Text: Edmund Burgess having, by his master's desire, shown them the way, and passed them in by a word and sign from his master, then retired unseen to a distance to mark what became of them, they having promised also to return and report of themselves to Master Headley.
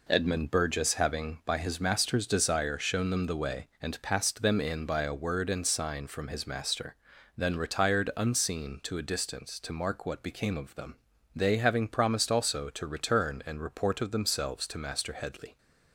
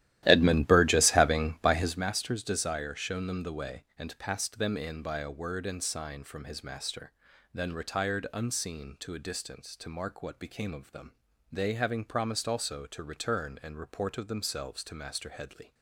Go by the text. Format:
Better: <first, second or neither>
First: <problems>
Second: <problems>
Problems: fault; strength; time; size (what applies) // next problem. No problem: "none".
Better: first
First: none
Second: starts louder than the rest; strong; until 2.1 s; 14 dB